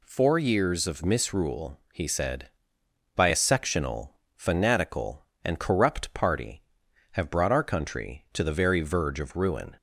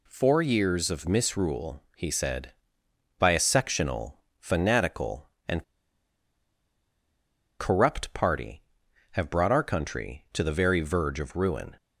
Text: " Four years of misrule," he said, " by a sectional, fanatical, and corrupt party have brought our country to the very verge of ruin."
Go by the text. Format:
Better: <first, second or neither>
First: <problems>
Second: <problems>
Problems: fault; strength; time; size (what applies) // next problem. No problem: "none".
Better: first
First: none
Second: pauses between "and" and "corrupt"; strong; at 5.6 s; 1.9 s long